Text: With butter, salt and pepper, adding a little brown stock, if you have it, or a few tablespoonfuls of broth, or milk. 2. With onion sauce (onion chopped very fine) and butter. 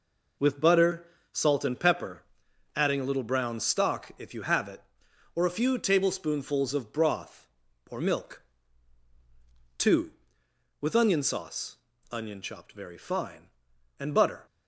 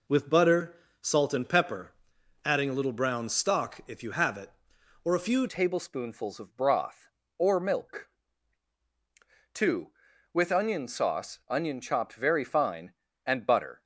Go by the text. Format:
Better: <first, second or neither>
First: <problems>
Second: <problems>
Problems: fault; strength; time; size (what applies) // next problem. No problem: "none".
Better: first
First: none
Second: changes voice at "tablespoonfuls"; from 5.4 s on; 8.4 s long